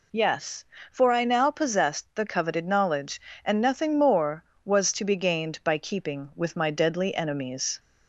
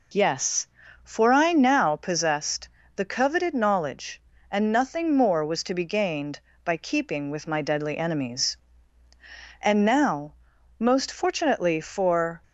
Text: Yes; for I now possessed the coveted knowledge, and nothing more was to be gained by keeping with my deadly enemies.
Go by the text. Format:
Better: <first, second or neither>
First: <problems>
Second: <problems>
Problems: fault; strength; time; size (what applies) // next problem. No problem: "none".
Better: first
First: none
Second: pauses between "possessed" and "the"; slight; at 2.6 s; 0.28 s long // goes on to say "And now most fortunately for"; strong; from 9.6 s on; 2.8 s long